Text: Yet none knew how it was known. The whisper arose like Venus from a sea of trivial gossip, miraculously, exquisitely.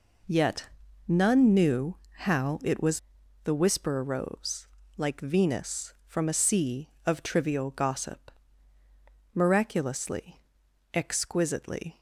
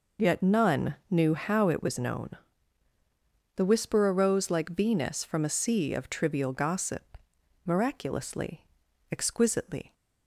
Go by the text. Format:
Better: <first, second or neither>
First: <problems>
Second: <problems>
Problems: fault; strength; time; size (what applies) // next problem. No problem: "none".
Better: second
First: pauses between "Yet" and "none"; at 0.6 s; 0.40 s long // pauses between "knew" and "how"; slight; at 1.9 s; 0.22 s long // skips "known"; at 3.2 s // pauses between "arose" and "like"; slight; at 4.6 s; 0.30 s long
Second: none